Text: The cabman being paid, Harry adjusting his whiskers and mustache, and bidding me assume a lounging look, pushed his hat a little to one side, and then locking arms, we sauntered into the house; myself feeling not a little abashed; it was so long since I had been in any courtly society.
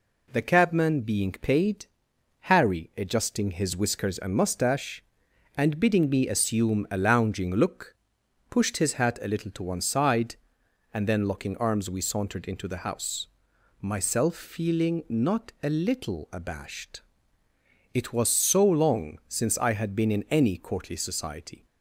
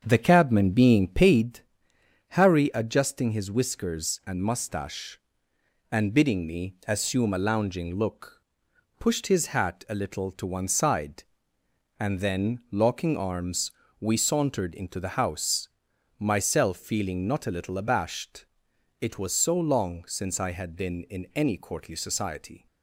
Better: first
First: none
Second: starts louder than the rest; strong; until 1.5 s; 7.5 dB

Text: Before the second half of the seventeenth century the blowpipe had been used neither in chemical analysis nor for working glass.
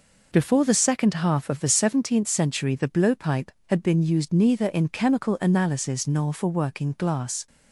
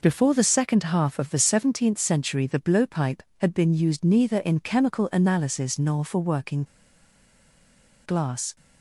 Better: first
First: none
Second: pauses between "working" and "glass"; strong; at 6.6 s; 1.4 s long

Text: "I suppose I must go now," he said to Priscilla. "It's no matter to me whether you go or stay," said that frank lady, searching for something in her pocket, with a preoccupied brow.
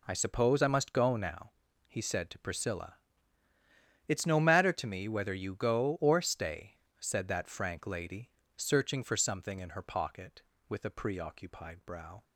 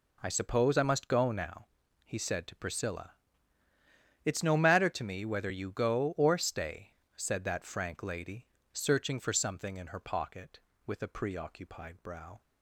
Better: neither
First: none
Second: none

